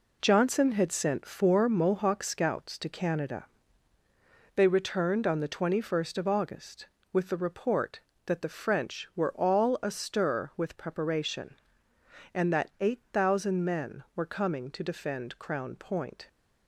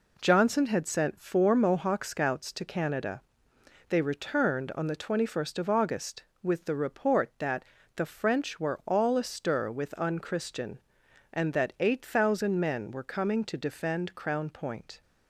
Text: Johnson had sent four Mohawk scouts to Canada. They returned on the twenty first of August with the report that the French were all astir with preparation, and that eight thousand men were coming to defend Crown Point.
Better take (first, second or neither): first